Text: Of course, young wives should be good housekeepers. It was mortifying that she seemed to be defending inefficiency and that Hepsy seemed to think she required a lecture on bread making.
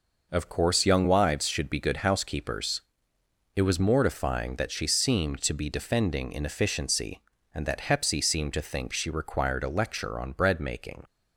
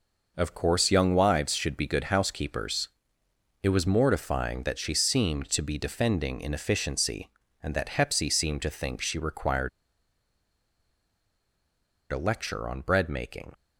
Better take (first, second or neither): first